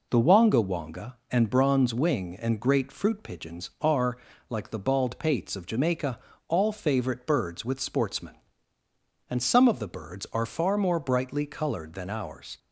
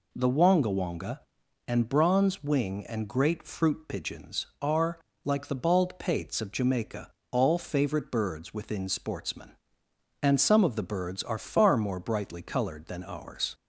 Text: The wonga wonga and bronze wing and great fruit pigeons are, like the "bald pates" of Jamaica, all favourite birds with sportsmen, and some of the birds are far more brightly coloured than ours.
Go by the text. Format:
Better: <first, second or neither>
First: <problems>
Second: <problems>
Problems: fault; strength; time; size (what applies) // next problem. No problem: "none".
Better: first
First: none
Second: says "within" for "with"; at 8.5 s